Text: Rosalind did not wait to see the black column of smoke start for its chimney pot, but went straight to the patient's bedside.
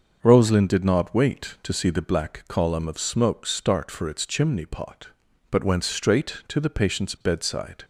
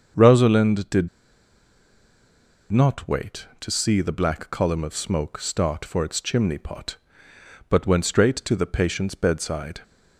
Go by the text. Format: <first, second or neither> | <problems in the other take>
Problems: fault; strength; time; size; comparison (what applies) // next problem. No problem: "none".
first | starts louder than the rest; until 2.8 s; 6.5 dB; also in the first // pauses between "did" and "not"; strong; at 1.0 s; 1.6 s long